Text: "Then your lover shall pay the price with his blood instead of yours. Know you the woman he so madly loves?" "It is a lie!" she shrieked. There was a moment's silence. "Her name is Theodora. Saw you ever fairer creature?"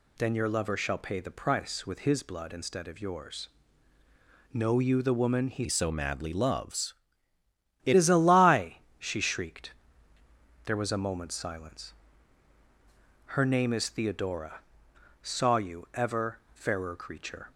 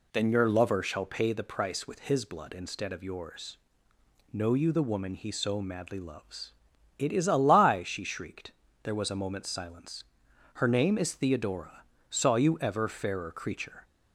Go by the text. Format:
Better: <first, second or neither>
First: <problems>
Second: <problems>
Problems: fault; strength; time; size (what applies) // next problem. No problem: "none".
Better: second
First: changes voice from "so" to "It"; from 5.6 to 7.9 s; 2.3 s long // pauses between "ever" and "fairer"; slight; at 16.3 s; 0.16 s long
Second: none